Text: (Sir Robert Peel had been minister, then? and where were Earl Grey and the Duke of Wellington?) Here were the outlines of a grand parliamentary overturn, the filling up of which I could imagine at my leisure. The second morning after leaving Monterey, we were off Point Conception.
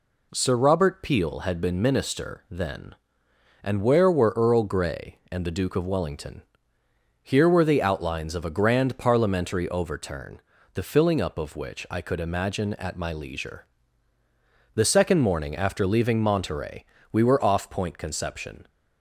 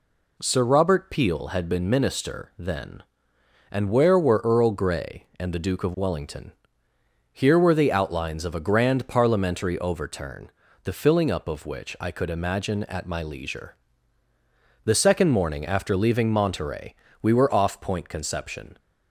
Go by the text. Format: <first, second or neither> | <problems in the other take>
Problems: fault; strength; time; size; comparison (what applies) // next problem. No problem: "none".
neither | none